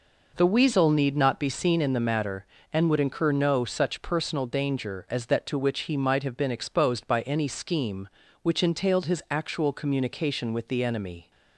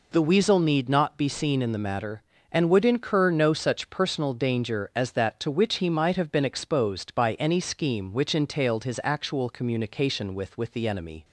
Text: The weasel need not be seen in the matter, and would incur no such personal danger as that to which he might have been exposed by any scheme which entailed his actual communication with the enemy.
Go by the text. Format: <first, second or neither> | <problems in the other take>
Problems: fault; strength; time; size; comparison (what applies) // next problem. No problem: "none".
first | says "with" twice; at 10.5 s